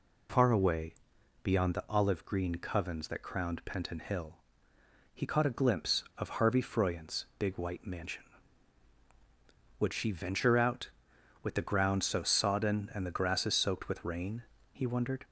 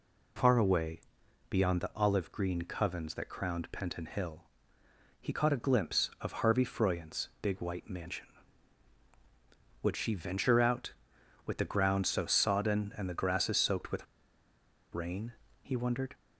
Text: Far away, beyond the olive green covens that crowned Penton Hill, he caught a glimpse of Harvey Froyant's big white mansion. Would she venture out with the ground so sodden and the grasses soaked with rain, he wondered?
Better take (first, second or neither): first